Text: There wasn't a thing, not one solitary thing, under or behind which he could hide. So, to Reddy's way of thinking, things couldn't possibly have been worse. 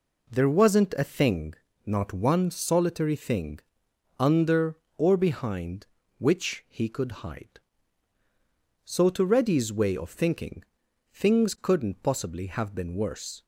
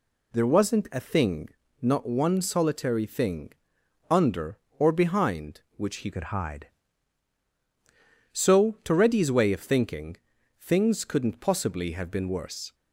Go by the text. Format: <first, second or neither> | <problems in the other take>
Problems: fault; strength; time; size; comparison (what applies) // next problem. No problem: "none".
first | changes voice from "could" to "hide"; from 6.1 to 6.6 s; 0.5 s long